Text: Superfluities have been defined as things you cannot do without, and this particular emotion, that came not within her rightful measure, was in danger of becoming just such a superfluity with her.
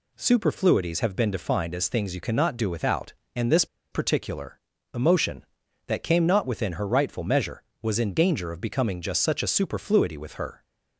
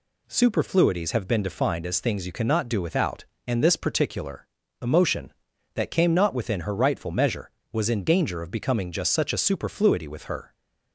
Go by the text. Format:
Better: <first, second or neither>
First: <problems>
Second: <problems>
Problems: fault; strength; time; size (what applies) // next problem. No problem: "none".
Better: second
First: pauses between "this" and "particular"; slight; at 3.6 s; 0.26 s long // pauses between "particular" and "emotion"; slight; at 4.5 s; 0.34 s long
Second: pauses between "particular" and "emotion"; slight; at 4.4 s; 0.34 s long